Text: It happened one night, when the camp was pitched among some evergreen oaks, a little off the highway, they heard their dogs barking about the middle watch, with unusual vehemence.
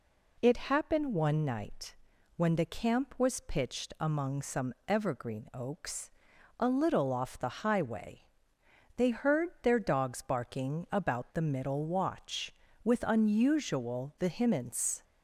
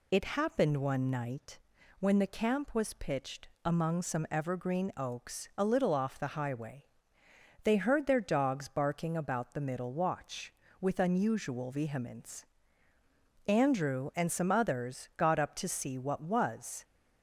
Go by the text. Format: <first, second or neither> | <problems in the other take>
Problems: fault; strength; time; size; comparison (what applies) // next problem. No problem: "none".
first | pauses between "pitched" and "among"; slight; at 3.4 s; 0.18 s long // goes on to say "Andrew and some others got up to see what was"; strong; from 13.4 s on; 3.3 s long